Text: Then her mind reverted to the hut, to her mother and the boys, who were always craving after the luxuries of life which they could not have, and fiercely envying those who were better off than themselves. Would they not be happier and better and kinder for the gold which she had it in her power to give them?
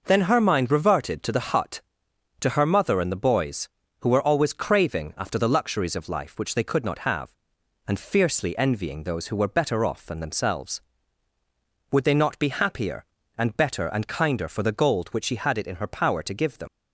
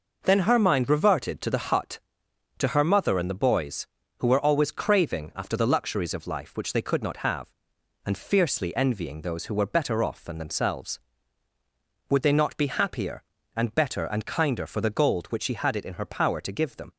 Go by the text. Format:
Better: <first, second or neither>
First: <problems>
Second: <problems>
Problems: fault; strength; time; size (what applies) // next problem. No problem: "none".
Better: second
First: leaves "them" unfinished; at 16.6 s; 50 ms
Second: none